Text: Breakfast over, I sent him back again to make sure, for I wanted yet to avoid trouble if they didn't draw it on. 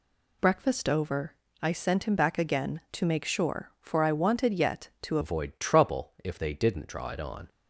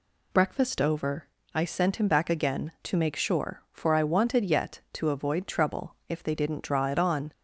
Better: second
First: changes voice at "avoid"; from 5.2 s on; 2.2 s long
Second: none

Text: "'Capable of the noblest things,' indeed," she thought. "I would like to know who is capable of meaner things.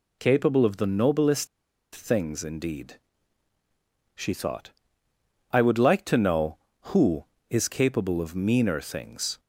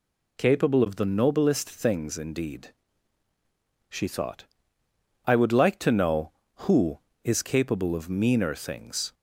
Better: second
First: pauses between "noblest" and "things"; noticeable; at 1.4 s; 0.47 s long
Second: none

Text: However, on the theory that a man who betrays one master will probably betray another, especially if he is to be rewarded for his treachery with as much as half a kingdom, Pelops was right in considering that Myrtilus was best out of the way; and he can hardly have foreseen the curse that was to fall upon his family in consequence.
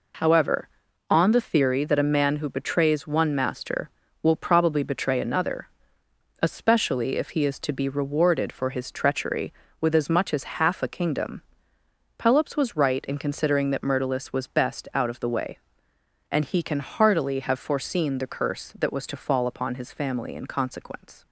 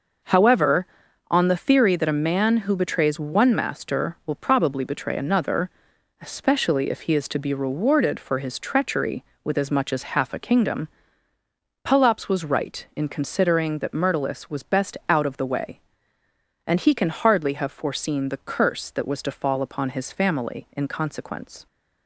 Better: second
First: says "heartily" for "hardly"; at 16.7 s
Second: none

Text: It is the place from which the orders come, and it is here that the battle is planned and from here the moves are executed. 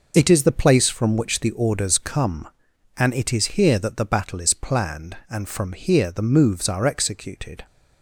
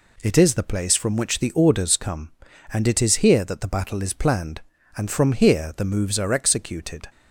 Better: neither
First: none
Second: none

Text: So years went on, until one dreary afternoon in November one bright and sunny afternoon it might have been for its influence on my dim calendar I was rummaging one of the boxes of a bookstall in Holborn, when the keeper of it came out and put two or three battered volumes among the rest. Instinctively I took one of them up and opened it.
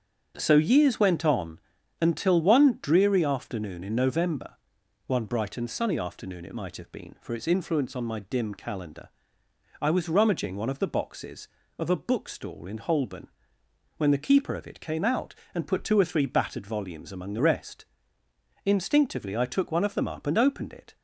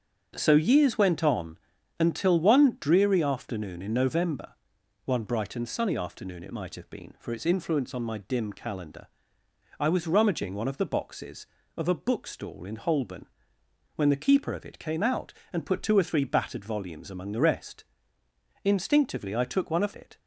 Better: first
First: starts louder than the rest; strong; until 1.3 s; 7 dB // pauses between "November" and "one"; noticeable; at 4.5 s; 0.50 s long // pauses between "calendar" and "I"; noticeable; at 9.0 s; 0.72 s long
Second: starts louder than the rest; strong; until 1.3 s; 7.5 dB // pauses between "November" and "one"; noticeable; at 4.5 s; 0.50 s long // pauses between "calendar" and "I"; noticeable; at 9.0 s; 0.72 s long // skips "them up and opened"; at 19.9 s

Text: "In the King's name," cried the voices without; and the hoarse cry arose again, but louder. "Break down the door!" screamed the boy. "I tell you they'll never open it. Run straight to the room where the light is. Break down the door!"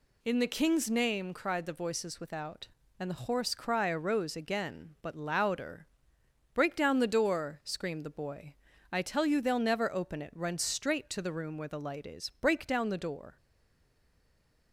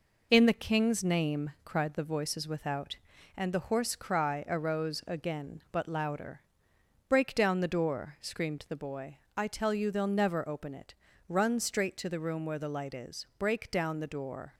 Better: second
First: stays silent after the last word; noticeable; from 13.3 s on; 1.4 s long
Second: none

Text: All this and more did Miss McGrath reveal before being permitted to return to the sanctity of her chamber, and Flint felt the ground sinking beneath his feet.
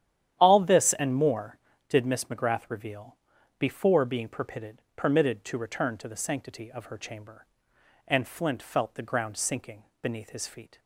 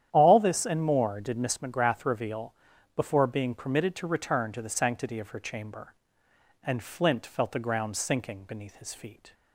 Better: second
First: starts louder than the rest; strong; until 1.3 s; 10.5 dB // pauses between "reveal" and "before"; at 3.1 s; 0.40 s long // says "permitted" twice; at 4.9 s // pauses between "sinking" and "beneath"; slight; at 9.8 s; 0.20 s long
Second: starts louder than the rest; strong; until 1.1 s; 10 dB // pauses between "reveal" and "before"; at 2.5 s; 0.42 s long

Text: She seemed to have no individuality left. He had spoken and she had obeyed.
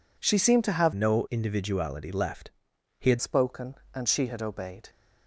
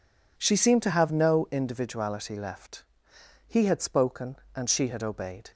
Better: second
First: changes voice from "no" to "had"; from 0.9 to 3.1 s; 2.2 s long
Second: none

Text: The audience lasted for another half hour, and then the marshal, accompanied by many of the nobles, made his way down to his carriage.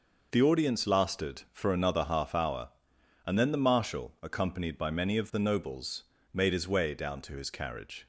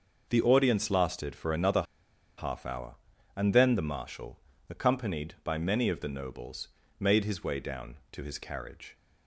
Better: first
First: none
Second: pauses between "another" and "half"; noticeable; at 1.8 s; 0.54 s long

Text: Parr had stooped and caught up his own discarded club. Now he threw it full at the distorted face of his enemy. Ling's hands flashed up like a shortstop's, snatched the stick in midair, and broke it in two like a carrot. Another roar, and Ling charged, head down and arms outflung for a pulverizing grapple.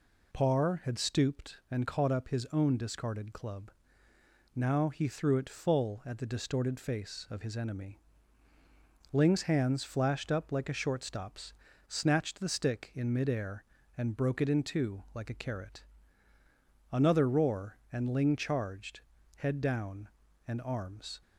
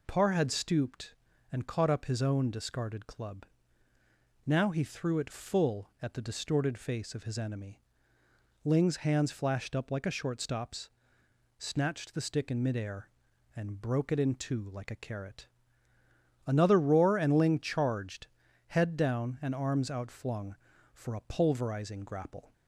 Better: second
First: stops before "outflung for a pulverizing grapple"; at 21.2 s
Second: none

